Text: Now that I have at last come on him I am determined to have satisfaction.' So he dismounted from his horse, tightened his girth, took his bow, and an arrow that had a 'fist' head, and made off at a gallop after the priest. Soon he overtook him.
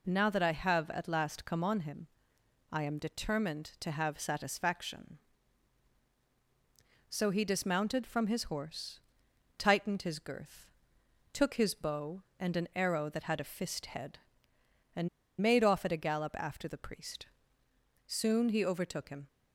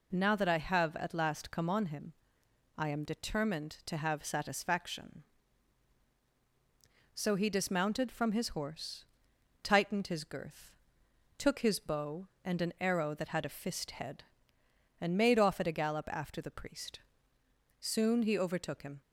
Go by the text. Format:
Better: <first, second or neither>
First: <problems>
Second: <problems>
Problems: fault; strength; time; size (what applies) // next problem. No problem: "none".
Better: second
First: pauses between "him" and "I"; noticeable; at 2.0 s; 0.66 s long // pauses between "and" and "made"; slight; at 15.0 s; 0.32 s long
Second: pauses between "him" and "I"; noticeable; at 2.1 s; 0.66 s long